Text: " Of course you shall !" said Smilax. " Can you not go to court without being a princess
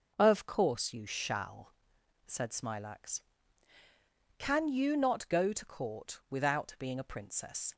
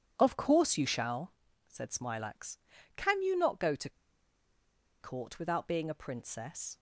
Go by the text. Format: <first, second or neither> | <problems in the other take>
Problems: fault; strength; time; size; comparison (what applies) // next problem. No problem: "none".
first | starts louder than the rest; strong; until 1.1 s; 8 dB // pauses between "to" and "court"; at 3.8 s; 1.1 s long